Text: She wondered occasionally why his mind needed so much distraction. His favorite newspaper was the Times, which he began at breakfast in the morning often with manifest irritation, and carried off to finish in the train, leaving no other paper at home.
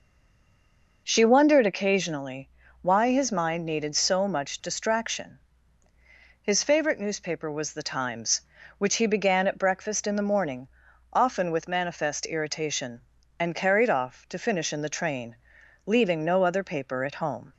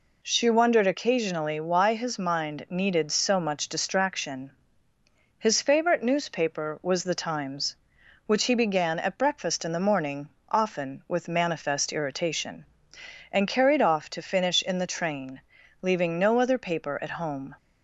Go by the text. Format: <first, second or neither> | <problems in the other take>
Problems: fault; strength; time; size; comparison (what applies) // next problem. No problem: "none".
second | stays silent before the first word; until 1.0 s; 1.0 s long // pauses between "occasionally" and "why"; slight; at 2.4 s; 0.32 s long // pauses between "morning" and "often"; noticeable; at 10.6 s; 0.46 s long; slight in the second